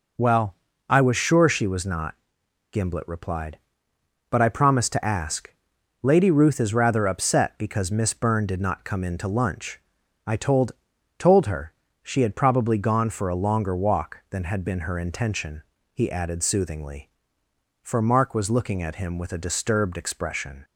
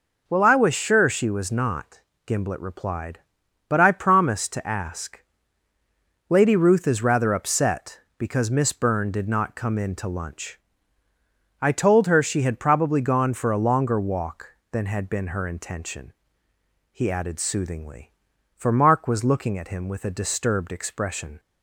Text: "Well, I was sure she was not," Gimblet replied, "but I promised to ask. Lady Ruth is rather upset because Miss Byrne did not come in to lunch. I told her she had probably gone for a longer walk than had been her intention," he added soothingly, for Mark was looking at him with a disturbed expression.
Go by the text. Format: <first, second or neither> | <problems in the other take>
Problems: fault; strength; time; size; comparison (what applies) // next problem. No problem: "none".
second | says "told" twice; at 11.1 s // pauses between "her" and "she"; slight; at 11.7 s; 0.28 s long